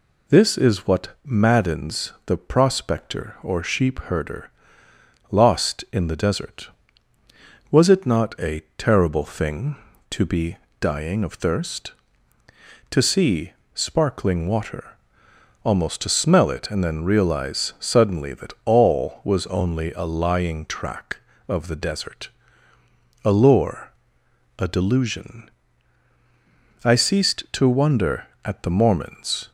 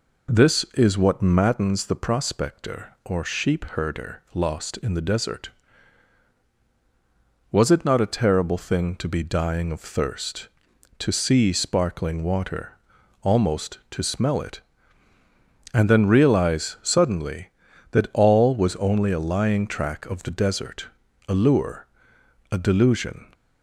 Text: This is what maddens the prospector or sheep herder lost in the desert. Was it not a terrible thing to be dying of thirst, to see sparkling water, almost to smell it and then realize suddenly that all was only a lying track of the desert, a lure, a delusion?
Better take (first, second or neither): second